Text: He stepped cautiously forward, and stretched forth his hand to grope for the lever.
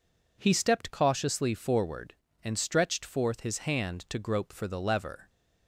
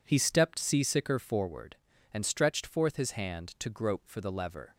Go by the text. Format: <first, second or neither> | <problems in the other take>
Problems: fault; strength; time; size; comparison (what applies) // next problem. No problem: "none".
first | says "seasicker" for "cautiously"; at 0.5 s